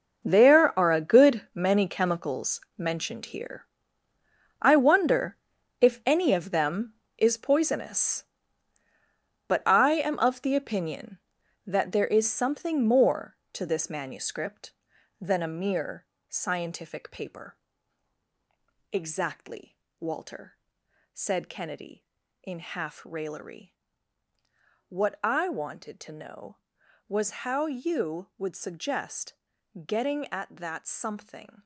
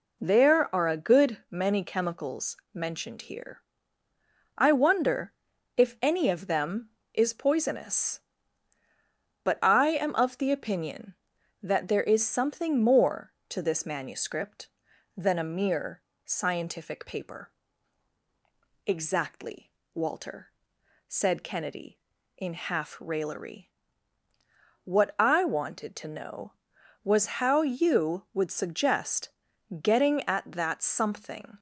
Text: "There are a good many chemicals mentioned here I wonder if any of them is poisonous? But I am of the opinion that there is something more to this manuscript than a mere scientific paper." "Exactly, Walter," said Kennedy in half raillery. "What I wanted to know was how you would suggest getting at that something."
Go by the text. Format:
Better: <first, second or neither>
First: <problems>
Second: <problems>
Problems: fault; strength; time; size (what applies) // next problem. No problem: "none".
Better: second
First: gets quieter; strong; throughout; 13 dB // pauses between "chemicals" and "mentioned"; slight; at 2.6 s; 0.18 s long // pauses between "here" and "I"; noticeable; at 3.6 s; 0.96 s long // pauses between "wonder" and "if"; at 5.3 s; 0.44 s long // pauses between "mere" and "scientific"; slight; at 16.0 s; 0.22 s long // pauses between "suggest" and "getting"; noticeable; at 29.3 s; 0.54 s long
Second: pauses between "chemicals" and "mentioned"; slight; at 2.5 s; 0.18 s long // pauses between "here" and "I"; noticeable; at 3.6 s; 0.96 s long // pauses between "wonder" and "if"; at 5.3 s; 0.44 s long // pauses between "mere" and "scientific"; slight; at 16.0 s; 0.22 s long // pauses between "suggest" and "getting"; noticeable; at 29.2 s; 0.54 s long